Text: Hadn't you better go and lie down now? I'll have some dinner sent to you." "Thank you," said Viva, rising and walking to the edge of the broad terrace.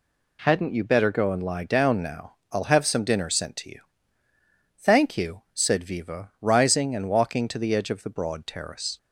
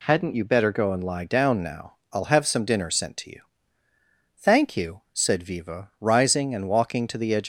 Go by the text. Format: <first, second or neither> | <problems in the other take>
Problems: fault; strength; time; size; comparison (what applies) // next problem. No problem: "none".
first | stops before "of the broad terrace"; at 7.4 s